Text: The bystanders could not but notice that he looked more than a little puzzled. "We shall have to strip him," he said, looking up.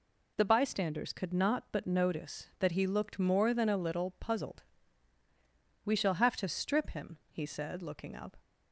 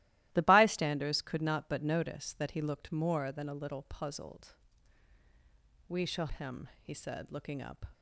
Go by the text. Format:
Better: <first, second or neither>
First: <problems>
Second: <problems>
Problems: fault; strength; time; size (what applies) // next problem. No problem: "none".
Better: first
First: none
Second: starts louder than the rest; strong; until 1.3 s; 16 dB // skips "have to strip"; at 6.2 s